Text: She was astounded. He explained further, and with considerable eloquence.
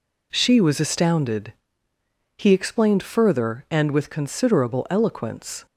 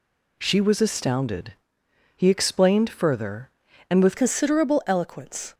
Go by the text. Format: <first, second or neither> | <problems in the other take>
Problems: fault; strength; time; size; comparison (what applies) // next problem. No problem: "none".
first | changes voice at "considerable"; from 4.1 s on; 1.4 s long